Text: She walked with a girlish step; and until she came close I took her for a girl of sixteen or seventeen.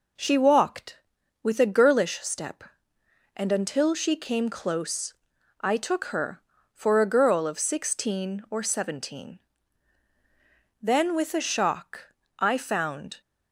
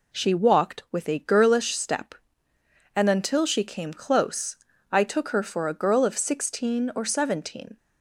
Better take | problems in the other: second | pauses between "close" and "I"; noticeable; at 5.1 s; 0.48 s long; slight in the second // goes on to say "Then with a shock I found"; strong; from 10.8 s on; 2.4 s long

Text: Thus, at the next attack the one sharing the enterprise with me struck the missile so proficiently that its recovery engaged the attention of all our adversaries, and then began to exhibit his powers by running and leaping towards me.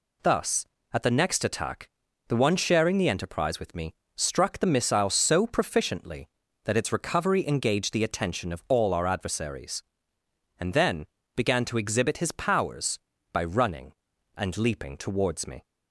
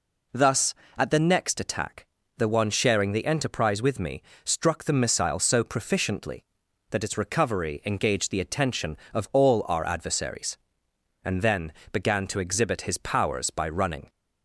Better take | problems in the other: first | pauses between "attack" and "the"; slight; at 2.0 s; 0.32 s long; also in the first // pauses between "me" and "struck"; slight; at 4.2 s; 0.24 s long; slight in the first // pauses between "then" and "began"; slight; at 11.7 s; 0.18 s long; slight in the first // stops before "and leaping towards me"; at 14.0 s

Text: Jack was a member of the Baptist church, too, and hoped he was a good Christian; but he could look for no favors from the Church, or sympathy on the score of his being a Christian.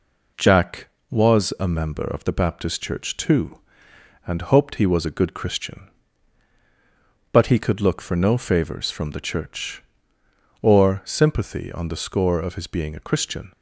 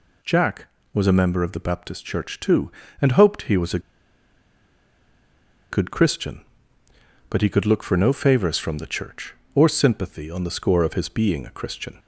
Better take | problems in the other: first | pauses between "a" and "good"; strong; at 3.7 s; 1.9 s long

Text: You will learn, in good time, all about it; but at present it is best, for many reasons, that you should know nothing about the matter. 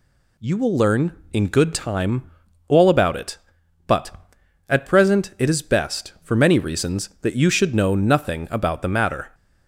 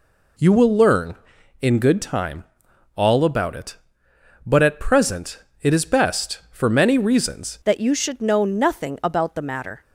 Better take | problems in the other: first | pauses between "present" and "it"; slight; at 5.4 s; 0.20 s long // changes voice at "that"; from 7.6 s on; 2.2 s long

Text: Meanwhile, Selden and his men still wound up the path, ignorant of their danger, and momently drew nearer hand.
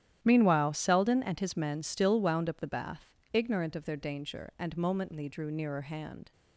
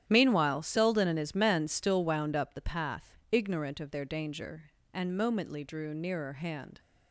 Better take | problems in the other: second | starts louder than the rest; strong; until 1.2 s; 11 dB; strong in the second // says "bath" for "path"; at 2.6 s

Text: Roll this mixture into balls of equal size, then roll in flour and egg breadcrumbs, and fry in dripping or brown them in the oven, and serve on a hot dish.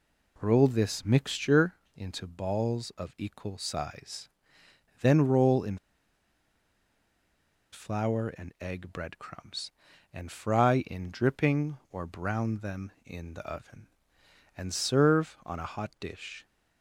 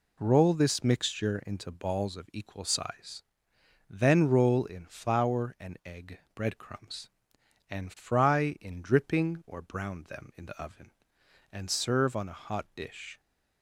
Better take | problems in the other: second | pauses between "mixture" and "into"; slight; at 1.7 s; 0.22 s long // pauses between "in" and "flour"; strong; at 5.7 s; 1.9 s long

